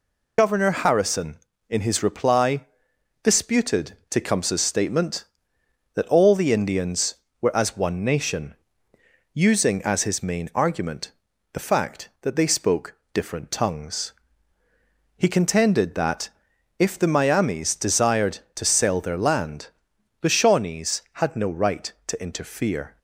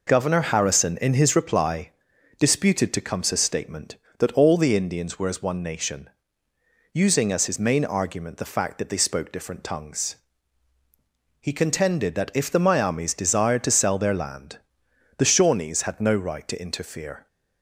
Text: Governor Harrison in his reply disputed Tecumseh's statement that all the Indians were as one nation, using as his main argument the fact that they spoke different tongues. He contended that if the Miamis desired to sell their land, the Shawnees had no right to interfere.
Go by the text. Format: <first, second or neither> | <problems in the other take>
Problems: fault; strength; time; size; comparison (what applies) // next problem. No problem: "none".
second | loses the start of "Governor"; at 0.3 s; 55 ms // pauses between "reply" and "disputed"; noticeable; at 2.6 s; 0.58 s long; noticeable in the second // pauses between "argument" and "the"; at 11.1 s; 0.42 s long // pauses between "spoke" and "different"; slight; at 12.9 s; 0.18 s long // pauses between "that" and "if"; noticeable; at 16.2 s; 0.50 s long